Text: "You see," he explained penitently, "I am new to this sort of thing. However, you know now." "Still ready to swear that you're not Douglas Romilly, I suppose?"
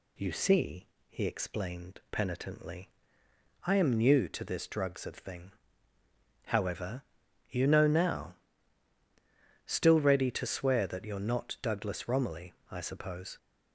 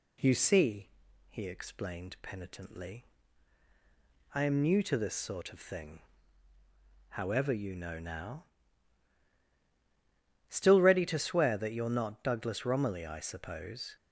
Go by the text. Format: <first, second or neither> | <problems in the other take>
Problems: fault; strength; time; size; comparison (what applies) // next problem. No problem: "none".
second | says "drugs" for "sort"; at 4.6 s